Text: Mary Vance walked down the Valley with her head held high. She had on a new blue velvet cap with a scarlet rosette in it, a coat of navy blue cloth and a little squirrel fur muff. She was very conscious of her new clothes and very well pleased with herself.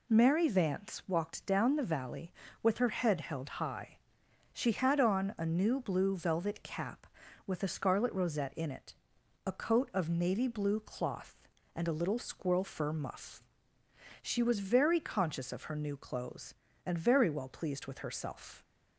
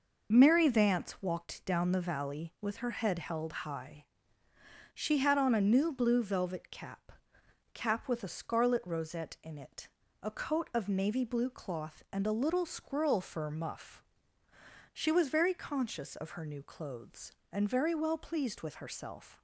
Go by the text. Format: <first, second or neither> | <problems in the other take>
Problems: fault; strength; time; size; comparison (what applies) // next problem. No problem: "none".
first | says "cap" twice; at 7.7 s